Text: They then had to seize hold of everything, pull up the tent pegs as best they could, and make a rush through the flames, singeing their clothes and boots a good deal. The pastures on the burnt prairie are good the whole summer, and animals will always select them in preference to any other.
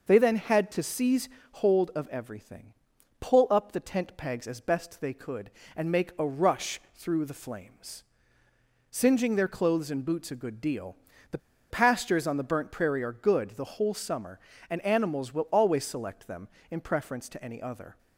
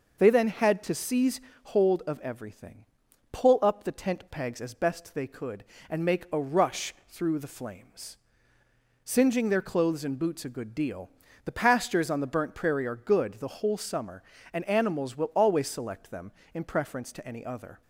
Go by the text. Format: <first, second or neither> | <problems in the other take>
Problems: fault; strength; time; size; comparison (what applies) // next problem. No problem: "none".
second | pauses between "seize" and "hold"; slight; at 1.2 s; 0.22 s long; slight in the second // pauses between "rush" and "through"; slight; at 6.7 s; 0.16 s long; slight in the second // pauses between "The" and "pastures"; slight; at 11.3 s; 0.33 s long